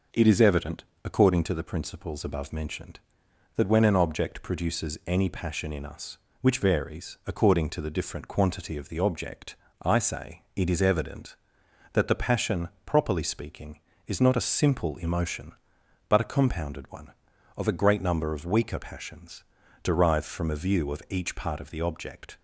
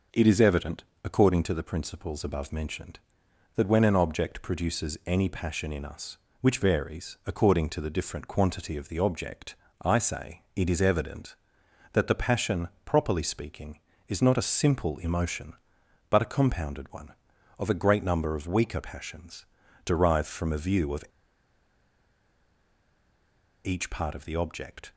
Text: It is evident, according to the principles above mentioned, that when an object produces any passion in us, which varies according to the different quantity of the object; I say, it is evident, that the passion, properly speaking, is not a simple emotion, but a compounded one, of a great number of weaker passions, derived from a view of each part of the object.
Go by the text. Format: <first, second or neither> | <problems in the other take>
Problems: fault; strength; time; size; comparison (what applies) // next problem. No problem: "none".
first | pauses between "of" and "each"; strong; at 21.0 s; 2.6 s long